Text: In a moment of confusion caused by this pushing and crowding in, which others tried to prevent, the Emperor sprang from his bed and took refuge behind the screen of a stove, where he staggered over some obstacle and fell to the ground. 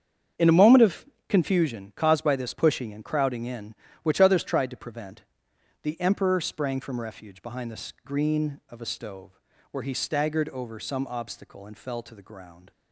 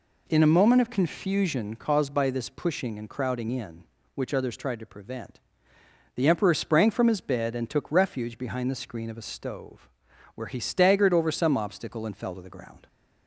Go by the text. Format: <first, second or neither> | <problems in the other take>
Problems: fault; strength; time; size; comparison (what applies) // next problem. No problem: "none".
second | starts louder than the rest; strong; until 1.6 s; 8 dB // pauses between "of" and "confusion"; slight; at 1.0 s; 0.24 s long // skips "his bed and took"; at 7.0 s